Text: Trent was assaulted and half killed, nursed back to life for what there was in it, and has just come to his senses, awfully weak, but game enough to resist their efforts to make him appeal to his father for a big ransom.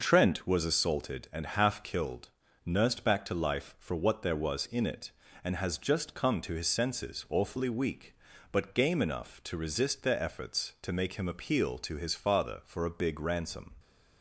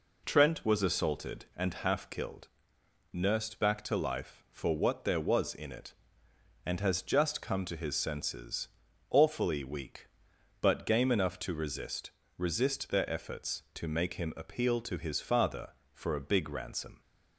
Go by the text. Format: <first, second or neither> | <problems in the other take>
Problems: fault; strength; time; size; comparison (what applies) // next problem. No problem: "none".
first | says "resist" twice; at 12.3 s